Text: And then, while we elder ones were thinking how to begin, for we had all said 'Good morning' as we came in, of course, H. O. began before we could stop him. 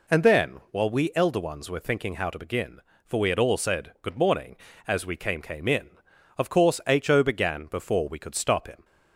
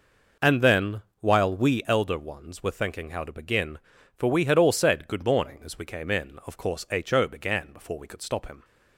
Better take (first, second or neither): second